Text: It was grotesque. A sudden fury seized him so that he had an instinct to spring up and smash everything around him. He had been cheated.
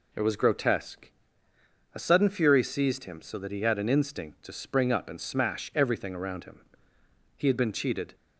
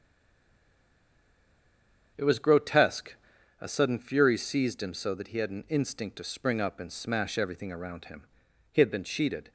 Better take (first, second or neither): first